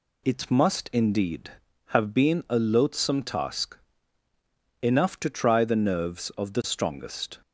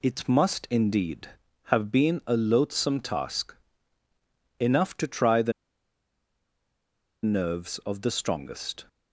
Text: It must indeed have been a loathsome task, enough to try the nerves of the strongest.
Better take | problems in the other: first | pauses between "the" and "nerves"; strong; at 5.5 s; 1.7 s long

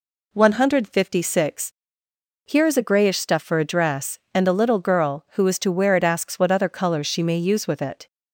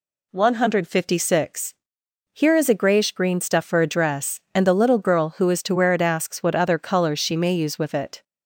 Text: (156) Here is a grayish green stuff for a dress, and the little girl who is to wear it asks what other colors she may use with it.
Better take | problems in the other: second | skips "green"; at 3.1 s

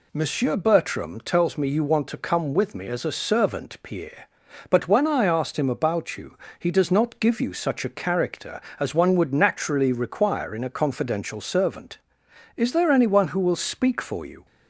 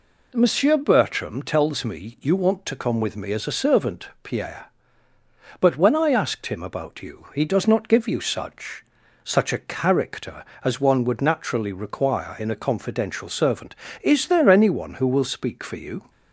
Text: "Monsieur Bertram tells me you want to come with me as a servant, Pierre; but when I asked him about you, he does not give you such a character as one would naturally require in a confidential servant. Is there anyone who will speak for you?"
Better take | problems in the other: first | says "such" twice; at 9.2 s

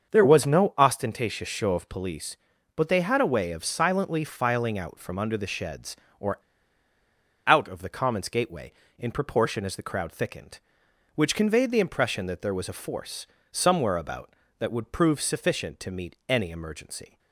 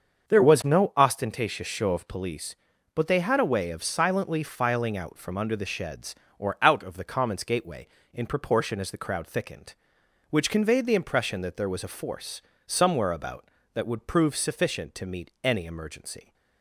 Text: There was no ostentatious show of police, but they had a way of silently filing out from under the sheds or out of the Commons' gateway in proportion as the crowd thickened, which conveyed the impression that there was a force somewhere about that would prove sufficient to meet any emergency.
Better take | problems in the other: second | starts louder than the rest; until 1.1 s; 6.5 dB; also in the second // pauses between "or" and "out"; at 6.3 s; 1.0 s long // pauses between "force" and "somewhere"; slight; at 13.2 s; 0.24 s long; slight in the second

